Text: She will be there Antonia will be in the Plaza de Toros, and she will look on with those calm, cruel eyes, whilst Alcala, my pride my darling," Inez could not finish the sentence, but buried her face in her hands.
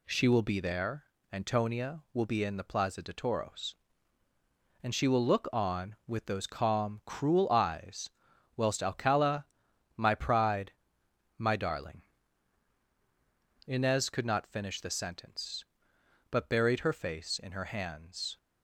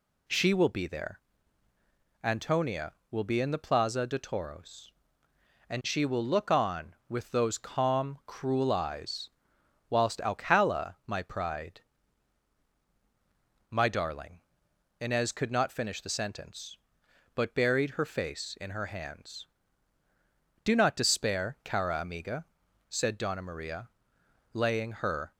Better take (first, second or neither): first